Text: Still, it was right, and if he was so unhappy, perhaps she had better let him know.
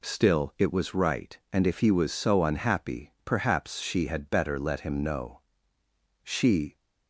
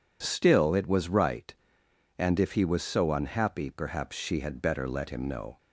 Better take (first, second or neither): second